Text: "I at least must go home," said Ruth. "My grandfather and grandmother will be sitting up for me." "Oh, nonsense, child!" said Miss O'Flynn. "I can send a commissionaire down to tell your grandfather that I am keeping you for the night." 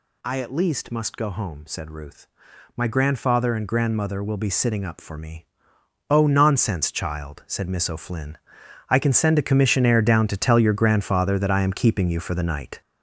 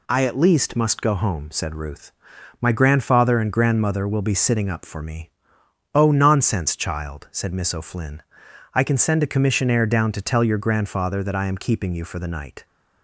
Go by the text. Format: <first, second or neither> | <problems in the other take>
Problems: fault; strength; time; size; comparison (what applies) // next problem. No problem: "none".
second | gets louder; throughout; 6 dB